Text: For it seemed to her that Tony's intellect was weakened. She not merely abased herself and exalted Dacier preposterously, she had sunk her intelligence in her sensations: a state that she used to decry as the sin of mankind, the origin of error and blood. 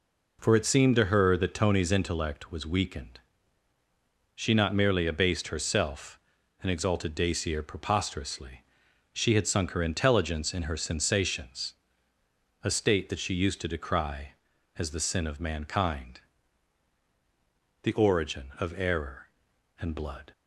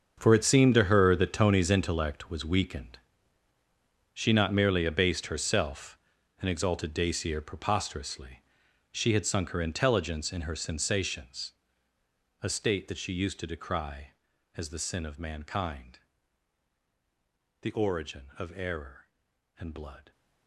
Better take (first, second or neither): first